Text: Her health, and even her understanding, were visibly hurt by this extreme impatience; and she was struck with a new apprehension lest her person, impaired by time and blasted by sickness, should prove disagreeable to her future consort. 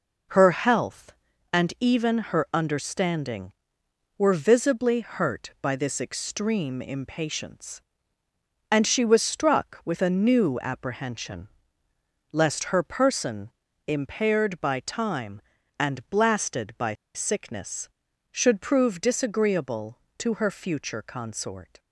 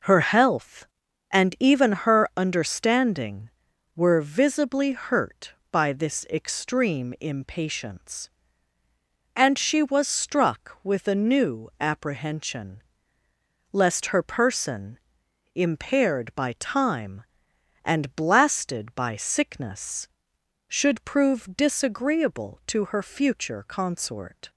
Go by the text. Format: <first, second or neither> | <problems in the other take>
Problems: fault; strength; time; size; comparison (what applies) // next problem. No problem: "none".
second | pauses between "apprehension" and "lest"; noticeable; at 11.4 s; 0.82 s long; noticeable in the second // pauses between "by" and "sickness"; slight; at 16.9 s; 0.22 s long